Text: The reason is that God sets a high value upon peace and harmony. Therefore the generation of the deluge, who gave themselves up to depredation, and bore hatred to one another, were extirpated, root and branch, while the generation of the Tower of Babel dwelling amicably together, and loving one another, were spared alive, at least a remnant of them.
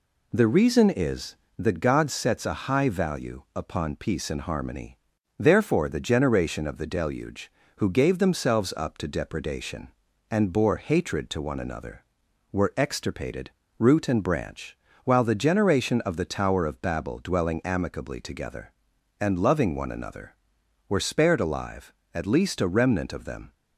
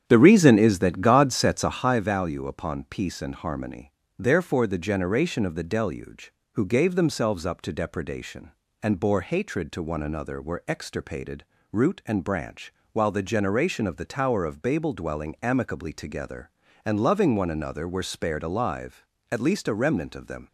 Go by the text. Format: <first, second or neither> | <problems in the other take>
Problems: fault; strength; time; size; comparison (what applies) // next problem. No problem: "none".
first | starts louder than the rest; strong; until 2.0 s; 9 dB